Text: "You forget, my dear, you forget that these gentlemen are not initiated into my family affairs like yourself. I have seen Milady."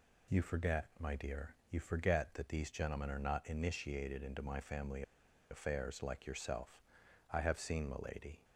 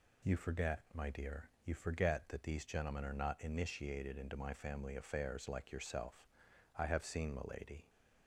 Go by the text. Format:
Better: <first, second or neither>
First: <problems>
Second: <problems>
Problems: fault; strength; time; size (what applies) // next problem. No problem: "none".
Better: second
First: pauses between "family" and "affairs"; noticeable; at 5.0 s; 0.48 s long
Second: none